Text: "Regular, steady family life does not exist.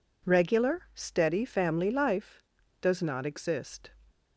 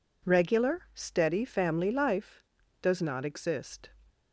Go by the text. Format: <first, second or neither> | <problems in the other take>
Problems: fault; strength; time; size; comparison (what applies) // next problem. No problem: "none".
neither | none